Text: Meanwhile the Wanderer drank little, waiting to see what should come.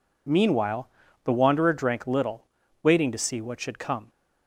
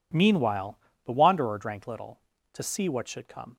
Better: first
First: pauses between "Meanwhile" and "the"; slight; at 0.8 s; 0.34 s long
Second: pauses between "Meanwhile" and "the"; slight; at 0.7 s; 0.28 s long // skips "waiting"; at 2.3 s

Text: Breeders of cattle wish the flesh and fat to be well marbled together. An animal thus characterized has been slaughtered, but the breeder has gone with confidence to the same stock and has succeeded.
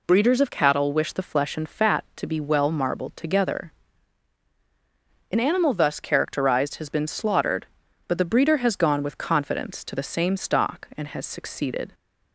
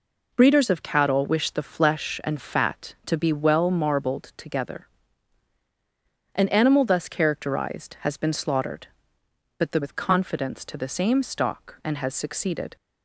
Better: first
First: none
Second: skips "breeder has gone"; at 9.8 s

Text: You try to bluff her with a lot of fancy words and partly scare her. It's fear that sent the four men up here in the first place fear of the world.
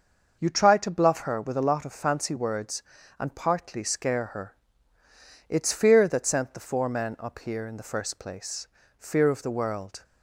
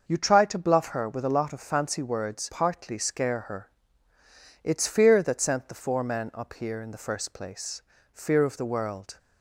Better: first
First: starts louder than the rest; until 1.4 s; 6 dB // pauses between "place" and "fear"; slight; at 8.6 s; 0.32 s long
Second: starts louder than the rest; until 1.0 s; 6 dB // skips "and"; at 2.5 s // pauses between "place" and "fear"; slight; at 7.8 s; 0.32 s long

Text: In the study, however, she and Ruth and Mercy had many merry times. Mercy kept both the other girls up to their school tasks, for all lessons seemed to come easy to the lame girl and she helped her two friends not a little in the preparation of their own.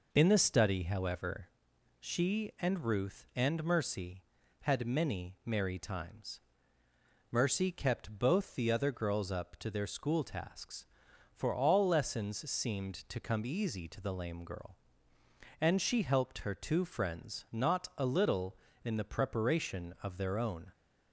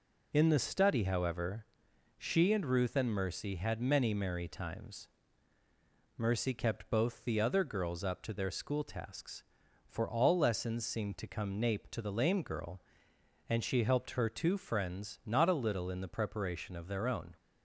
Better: first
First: none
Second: says "nape" for "easy"; at 11.5 s

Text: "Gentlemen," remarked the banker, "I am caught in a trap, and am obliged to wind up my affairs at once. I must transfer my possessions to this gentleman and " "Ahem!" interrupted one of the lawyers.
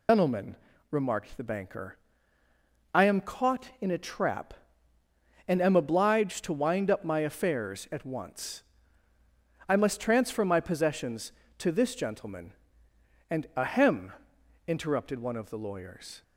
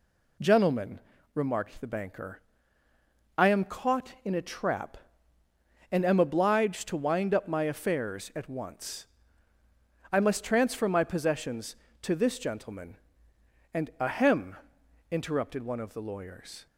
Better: second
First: loses the start of "Gentlemen"; at 0.0 s; 130 ms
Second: none

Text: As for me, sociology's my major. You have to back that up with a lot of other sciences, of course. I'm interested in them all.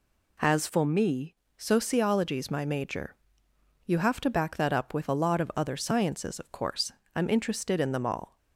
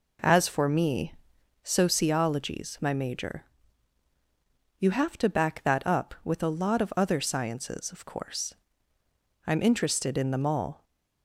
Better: second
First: changes voice from "for" to "me"; from 0.6 to 1.3 s; 0.7 s long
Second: none

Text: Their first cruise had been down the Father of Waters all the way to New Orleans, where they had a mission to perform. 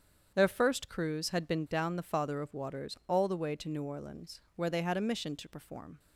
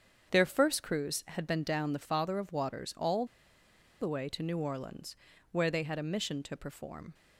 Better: first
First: starts louder than the rest; strong; until 1.3 s; 8 dB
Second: starts louder than the rest; strong; until 1.3 s; 7.5 dB // pauses between "all" and "the"; noticeable; at 3.2 s; 0.76 s long

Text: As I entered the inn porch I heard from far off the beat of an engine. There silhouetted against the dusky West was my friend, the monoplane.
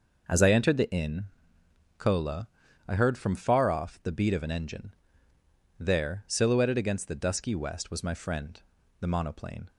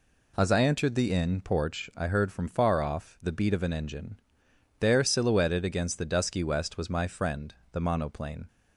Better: second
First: says "cola" for "porch"; at 1.9 s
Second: none

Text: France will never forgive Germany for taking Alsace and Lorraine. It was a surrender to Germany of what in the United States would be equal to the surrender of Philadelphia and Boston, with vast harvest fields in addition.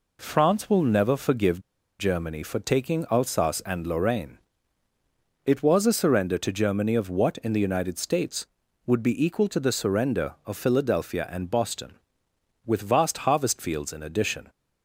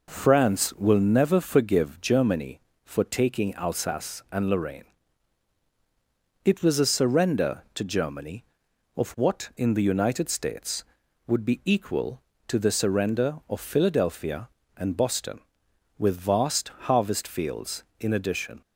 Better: second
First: pauses between "forgive" and "Germany"; at 1.6 s; 0.37 s long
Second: none

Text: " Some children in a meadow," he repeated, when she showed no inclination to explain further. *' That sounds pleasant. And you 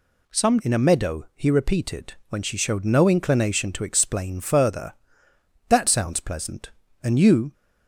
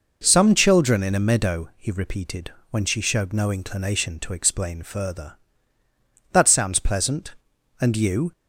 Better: second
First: skips "children"; at 0.6 s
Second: none

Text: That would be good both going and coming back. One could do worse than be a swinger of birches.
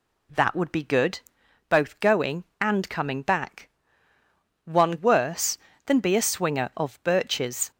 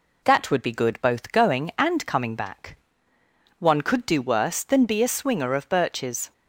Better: second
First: pauses between "good" and "both"; noticeable; at 1.2 s; 0.48 s long // skips "could do"; at 4.9 s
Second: none

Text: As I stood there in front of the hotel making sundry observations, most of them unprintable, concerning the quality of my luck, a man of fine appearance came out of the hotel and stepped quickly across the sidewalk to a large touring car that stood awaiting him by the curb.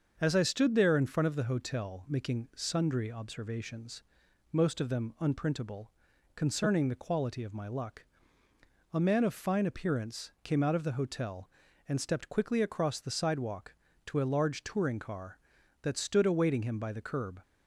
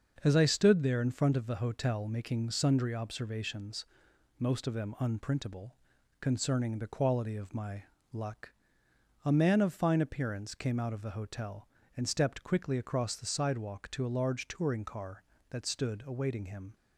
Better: first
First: starts louder than the rest; until 1.2 s; 6.5 dB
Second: starts louder than the rest; until 1.2 s; 6.5 dB // pauses between "my" and "luck"; slight; at 7.8 s; 0.28 s long // stops before "by the curb"; at 16.7 s

